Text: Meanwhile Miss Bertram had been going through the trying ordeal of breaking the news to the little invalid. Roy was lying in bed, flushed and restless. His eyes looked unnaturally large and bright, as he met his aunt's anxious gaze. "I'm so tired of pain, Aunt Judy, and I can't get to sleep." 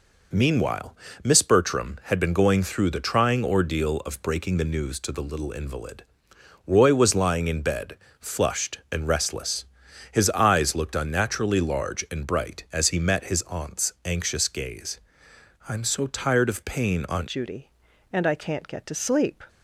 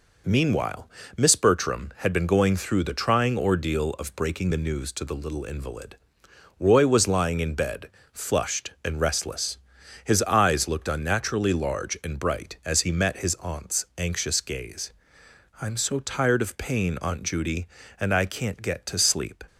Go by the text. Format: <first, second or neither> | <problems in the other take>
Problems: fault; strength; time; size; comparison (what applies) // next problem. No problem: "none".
second | pauses between "Meanwhile" and "Miss"; slight; at 0.9 s; 0.30 s long; slight in the second // changes voice at "Judy"; from 17.2 s on; 2.2 s long